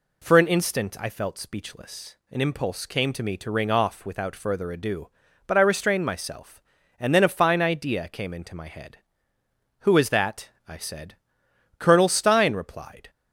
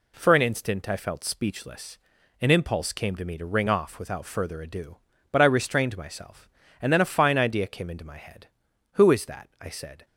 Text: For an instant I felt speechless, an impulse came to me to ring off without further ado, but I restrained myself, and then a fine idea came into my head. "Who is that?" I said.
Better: second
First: goes on to say "Colonel Stein replied"; noticeable; from 11.7 s on; 1.3 s long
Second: none

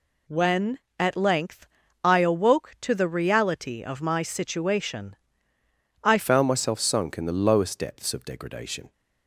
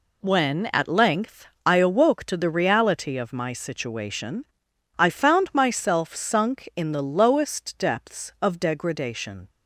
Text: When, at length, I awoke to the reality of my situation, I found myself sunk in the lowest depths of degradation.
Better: second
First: changes voice at "found"; from 6.1 s on; 2.8 s long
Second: none

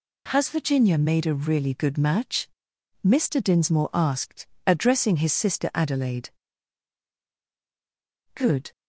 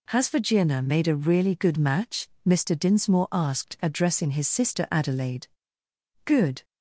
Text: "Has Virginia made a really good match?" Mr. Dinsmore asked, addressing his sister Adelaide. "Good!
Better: neither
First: none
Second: none

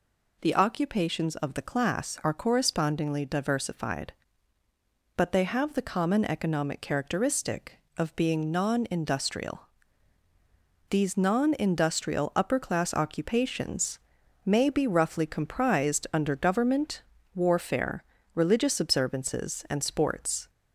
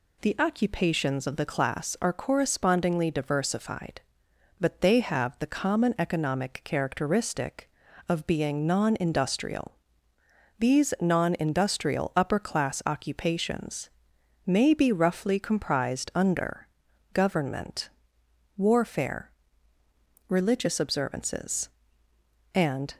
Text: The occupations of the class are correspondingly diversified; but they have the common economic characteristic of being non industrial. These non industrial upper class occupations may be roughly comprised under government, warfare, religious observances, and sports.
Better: first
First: pauses between "occupations" and "may"; noticeable; at 13.9 s; 0.48 s long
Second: pauses between "occupations" and "may"; noticeable; at 13.8 s; 0.56 s long // pauses between "under" and "government"; noticeable; at 16.6 s; 0.46 s long // stops before "sports"; at 22.9 s

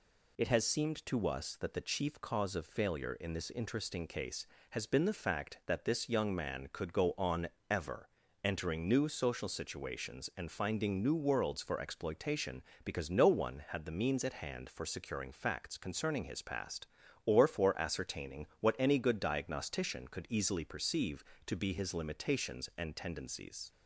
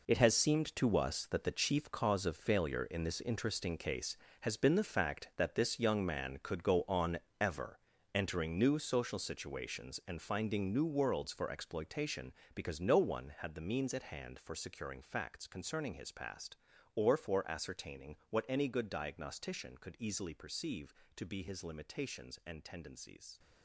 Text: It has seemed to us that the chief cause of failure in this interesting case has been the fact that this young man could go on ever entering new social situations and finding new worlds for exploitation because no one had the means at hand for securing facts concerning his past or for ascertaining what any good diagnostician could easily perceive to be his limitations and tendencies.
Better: first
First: pauses between "on" and "ever"; slight; at 7.4 s; 0.24 s long // pauses between "ever" and "entering"; slight; at 8.0 s; 0.34 s long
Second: gets quieter; strong; throughout; 12 dB // pauses between "on" and "ever"; slight; at 7.1 s; 0.24 s long // pauses between "ever" and "entering"; slight; at 7.7 s; 0.34 s long

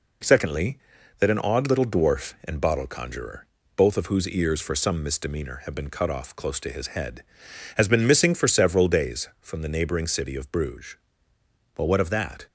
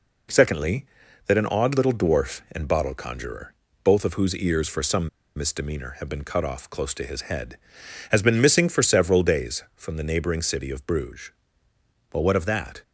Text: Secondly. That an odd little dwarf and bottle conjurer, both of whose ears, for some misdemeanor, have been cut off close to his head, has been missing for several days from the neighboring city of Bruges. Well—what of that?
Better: first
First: none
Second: pauses between "some" and "misdemeanor"; slight; at 5.0 s; 0.28 s long

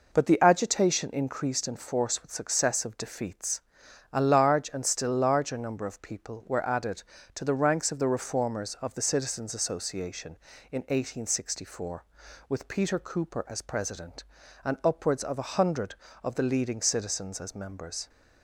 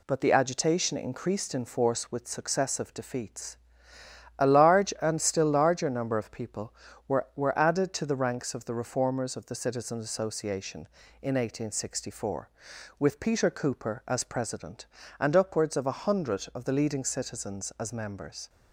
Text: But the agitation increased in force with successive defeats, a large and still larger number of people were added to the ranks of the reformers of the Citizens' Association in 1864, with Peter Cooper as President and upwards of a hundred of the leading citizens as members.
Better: first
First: none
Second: says "were" twice; at 7.3 s

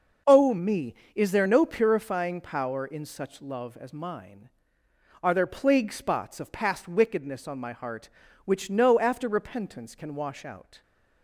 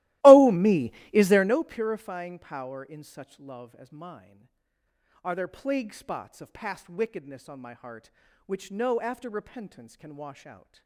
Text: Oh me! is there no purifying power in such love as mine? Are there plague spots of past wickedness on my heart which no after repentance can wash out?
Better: first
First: none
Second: starts louder than the rest; strong; until 1.6 s; 17.5 dB

